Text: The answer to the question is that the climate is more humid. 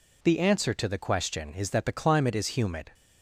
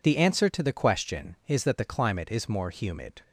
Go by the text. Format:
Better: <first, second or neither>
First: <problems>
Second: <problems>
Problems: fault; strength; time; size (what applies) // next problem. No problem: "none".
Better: second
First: skips "more"; at 2.4 s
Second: none